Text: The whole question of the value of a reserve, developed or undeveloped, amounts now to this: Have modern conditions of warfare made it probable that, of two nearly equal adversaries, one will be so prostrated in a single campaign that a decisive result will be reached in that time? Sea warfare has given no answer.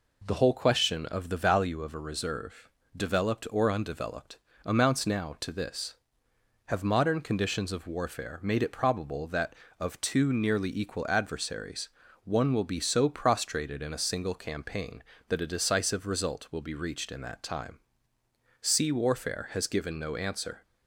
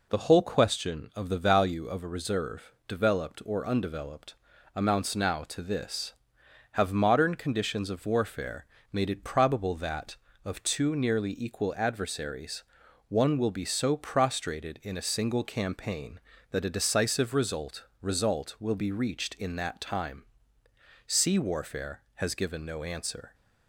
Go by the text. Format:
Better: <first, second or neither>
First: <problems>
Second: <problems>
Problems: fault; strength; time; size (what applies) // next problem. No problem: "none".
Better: first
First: none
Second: pauses between "warfare" and "made"; slight; at 8.6 s; 0.26 s long // says "result" twice; at 18.0 s